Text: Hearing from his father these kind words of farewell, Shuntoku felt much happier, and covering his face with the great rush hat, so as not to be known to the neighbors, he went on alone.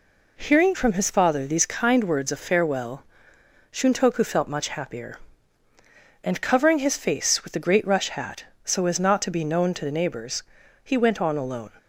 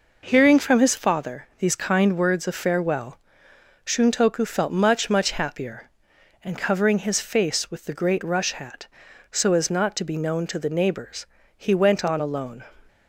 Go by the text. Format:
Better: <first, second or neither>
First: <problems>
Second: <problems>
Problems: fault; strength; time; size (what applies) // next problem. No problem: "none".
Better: first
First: none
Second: says "much" twice; at 5.0 s